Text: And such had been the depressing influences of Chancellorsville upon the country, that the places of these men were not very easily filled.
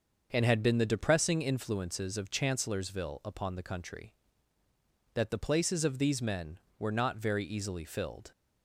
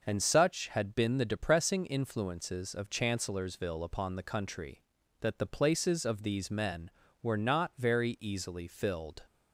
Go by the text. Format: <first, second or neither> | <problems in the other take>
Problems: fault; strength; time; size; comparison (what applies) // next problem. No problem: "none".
second | starts louder than the rest; until 1.3 s; 6.5 dB // skips "such"; at 0.4 s